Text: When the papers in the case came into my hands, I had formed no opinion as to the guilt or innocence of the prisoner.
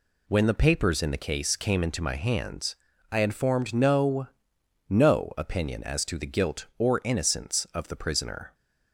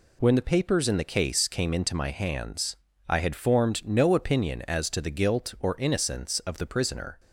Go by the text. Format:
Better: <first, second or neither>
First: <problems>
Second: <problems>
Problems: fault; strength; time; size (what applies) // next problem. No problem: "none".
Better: second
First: says "no" twice; at 4.8 s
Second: none